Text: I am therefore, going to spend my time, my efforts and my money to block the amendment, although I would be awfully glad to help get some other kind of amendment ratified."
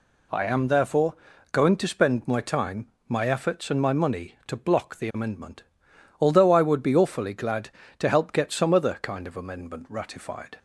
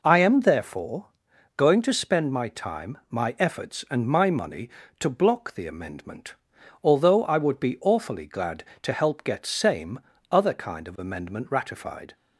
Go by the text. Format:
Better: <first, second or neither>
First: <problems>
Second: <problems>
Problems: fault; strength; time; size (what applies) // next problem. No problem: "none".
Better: first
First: none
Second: says "same" for "some"; at 9.4 s